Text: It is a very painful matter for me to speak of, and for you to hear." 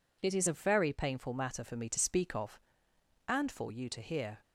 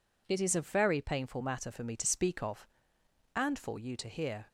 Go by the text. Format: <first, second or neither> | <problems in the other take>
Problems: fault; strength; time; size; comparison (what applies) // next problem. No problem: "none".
neither | none